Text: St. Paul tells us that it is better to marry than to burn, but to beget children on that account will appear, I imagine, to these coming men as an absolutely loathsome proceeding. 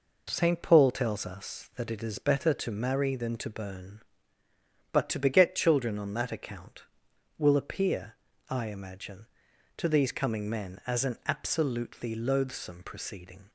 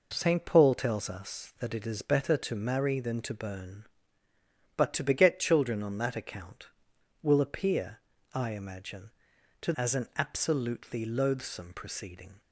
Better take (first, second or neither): first